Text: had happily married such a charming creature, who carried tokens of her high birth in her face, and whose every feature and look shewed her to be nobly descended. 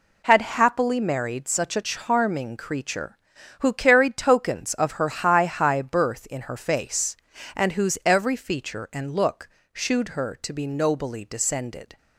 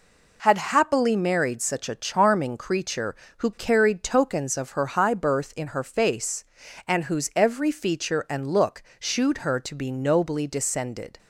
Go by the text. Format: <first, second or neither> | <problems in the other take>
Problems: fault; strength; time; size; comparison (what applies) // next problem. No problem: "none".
second | says "high" twice; at 5.4 s // pauses between "look" and "shewed"; slight; at 9.4 s; 0.24 s long; slight in the second